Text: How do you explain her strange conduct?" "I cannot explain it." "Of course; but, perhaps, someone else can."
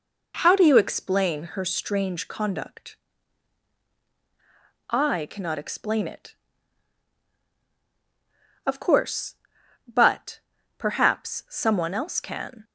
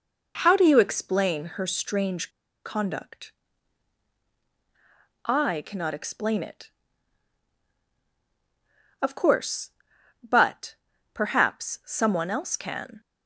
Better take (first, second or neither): first